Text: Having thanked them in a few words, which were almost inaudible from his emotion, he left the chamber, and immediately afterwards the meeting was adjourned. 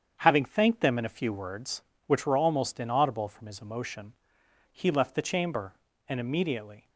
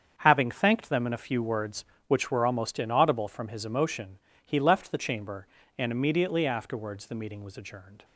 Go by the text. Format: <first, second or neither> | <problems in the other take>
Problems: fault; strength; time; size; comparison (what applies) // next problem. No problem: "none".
second | starts louder than the rest; strong; until 1.2 s; 8 dB; strong in the second // stops before "afterwards the meeting was adjourned"; at 6.8 s